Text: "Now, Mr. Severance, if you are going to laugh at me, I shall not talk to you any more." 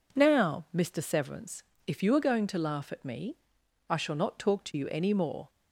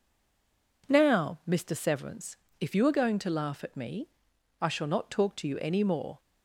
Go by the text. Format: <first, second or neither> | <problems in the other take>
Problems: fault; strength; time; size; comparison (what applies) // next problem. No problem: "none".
first | stays silent before the first word; slight; until 0.8 s; 0.8 s long